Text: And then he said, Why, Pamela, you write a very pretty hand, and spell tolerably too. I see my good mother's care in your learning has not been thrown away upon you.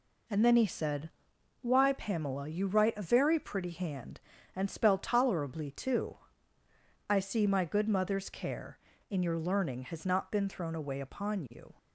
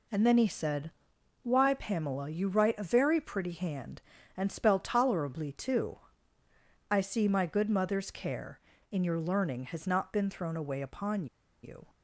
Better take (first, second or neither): first